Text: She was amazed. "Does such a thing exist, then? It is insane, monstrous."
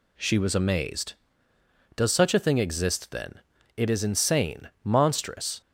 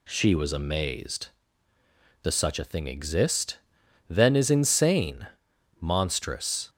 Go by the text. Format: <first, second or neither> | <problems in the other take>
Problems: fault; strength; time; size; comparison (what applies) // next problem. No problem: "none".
first | skips "It"; at 4.3 s